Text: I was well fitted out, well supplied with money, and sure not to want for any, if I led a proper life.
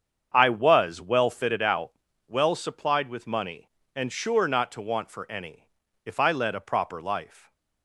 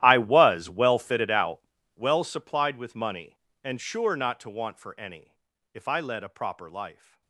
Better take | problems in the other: first | gets quieter; strong; throughout; 21.5 dB // starts louder than the rest; strong; until 1.0 s; 13 dB; strong in the first

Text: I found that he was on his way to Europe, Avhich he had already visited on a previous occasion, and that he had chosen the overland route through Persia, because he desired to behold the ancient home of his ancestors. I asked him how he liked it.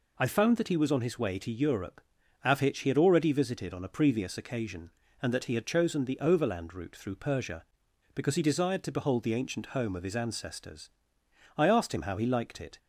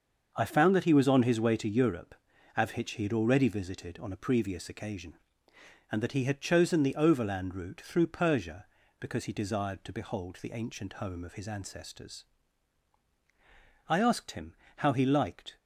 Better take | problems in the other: first | starts louder than the rest; until 1.3 s; 6.5 dB // pauses between "him" and "how"; slight; at 14.5 s; 0.22 s long // stops before "it"; at 15.5 s

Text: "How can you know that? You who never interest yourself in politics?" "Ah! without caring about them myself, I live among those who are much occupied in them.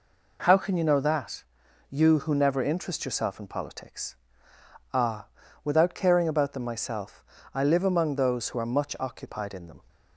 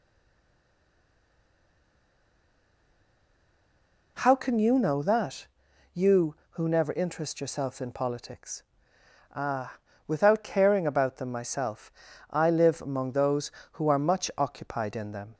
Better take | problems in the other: first | stays silent before the first word; strong; until 4.1 s; 4.1 s long

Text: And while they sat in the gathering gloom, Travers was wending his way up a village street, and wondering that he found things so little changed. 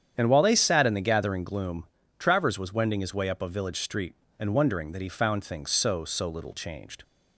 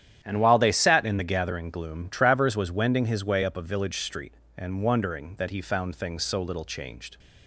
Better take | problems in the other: second | starts louder than the rest; strong; until 1.1 s; 9 dB; strong in the second // says "so" twice; at 6.0 s

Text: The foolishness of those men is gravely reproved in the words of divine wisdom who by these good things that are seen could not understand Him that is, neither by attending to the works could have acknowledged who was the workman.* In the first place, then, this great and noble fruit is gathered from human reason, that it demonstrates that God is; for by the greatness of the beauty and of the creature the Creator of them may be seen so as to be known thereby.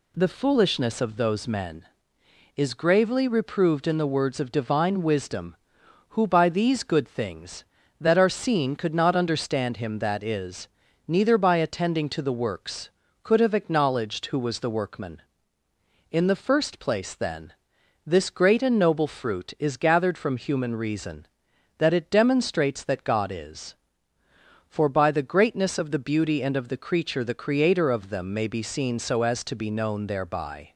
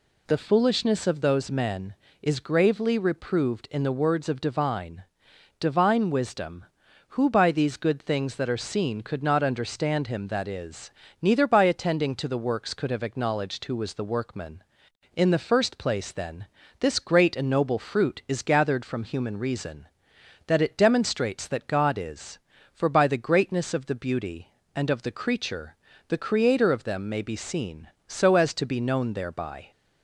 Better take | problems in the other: first | says "divine" twice; at 5.6 s // pauses between "creature" and "the"; slight; at 25.7 s; 0.32 s long

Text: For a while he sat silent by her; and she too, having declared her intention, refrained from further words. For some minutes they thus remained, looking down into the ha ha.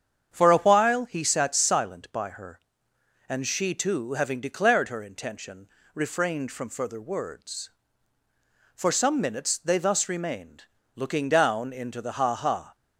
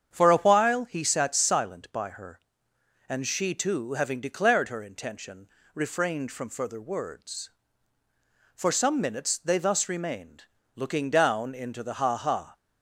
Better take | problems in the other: neither | starts louder than the rest; strong; the same in both

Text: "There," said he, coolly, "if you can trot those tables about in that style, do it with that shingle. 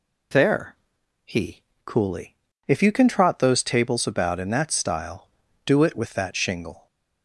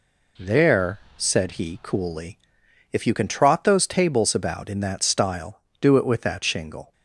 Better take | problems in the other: second | skips "said"; at 1.0 s

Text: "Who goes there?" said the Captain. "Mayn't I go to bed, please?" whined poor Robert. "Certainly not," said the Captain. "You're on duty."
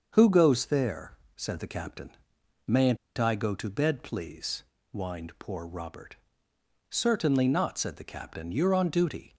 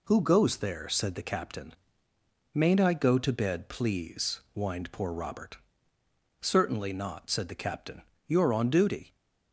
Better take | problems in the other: second | starts louder than the rest; until 1.1 s; 6.5 dB // pauses between "Mayn't" and "I"; slight; at 2.9 s; 0.21 s long

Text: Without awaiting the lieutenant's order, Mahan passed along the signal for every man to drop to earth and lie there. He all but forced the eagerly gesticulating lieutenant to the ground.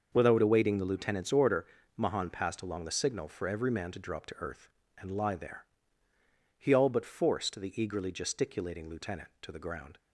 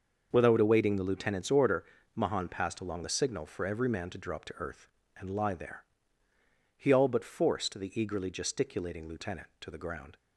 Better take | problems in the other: neither | starts louder than the rest; the same in both

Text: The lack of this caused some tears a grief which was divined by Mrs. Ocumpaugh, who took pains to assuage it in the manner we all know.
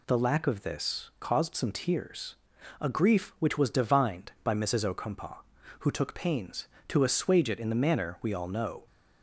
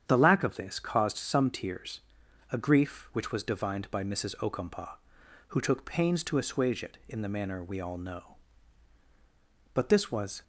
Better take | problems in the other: first | starts louder than the rest; strong; until 1.0 s; 8.5 dB // pauses between "tears" and "a"; noticeable; at 2.0 s; 0.52 s long; noticeable in the first // goes on to say "But this was"; noticeable; from 9.7 s on; 0.68 s long

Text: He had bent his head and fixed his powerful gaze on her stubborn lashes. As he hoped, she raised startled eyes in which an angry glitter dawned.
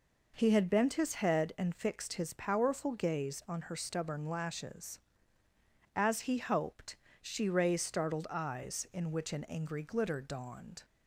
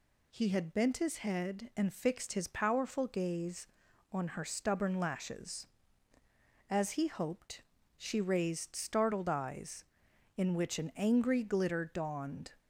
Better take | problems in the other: neither | none

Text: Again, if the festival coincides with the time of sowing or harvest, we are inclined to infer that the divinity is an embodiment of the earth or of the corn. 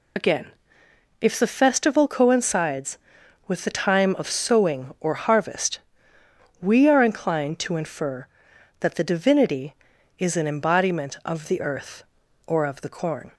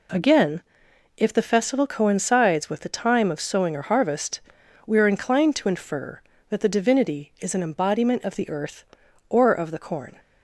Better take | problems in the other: second | loses the start of "Again"; at 0.1 s; 65 ms

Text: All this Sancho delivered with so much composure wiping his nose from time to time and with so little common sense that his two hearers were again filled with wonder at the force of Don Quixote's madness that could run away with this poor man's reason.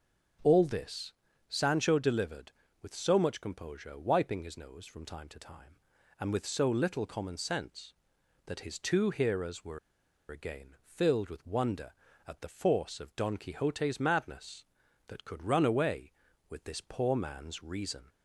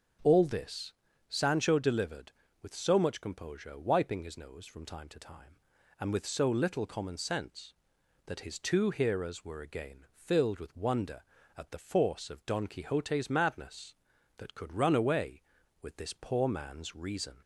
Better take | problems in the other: second | starts louder than the rest; until 1.8 s; 6 dB; also in the second // pauses between "this" and "Sancho"; at 1.1 s; 0.38 s long; also in the second // pauses between "were" and "again"; noticeable; at 9.7 s; 0.51 s long

